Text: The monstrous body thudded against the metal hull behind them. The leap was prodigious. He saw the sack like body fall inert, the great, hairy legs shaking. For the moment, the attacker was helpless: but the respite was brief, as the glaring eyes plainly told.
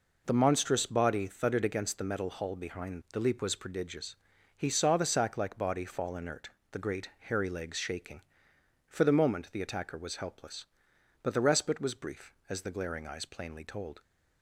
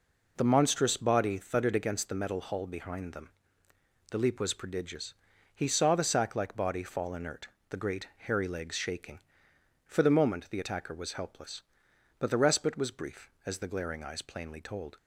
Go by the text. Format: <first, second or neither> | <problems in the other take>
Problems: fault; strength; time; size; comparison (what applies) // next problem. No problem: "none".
second | skips "them"; at 3.0 s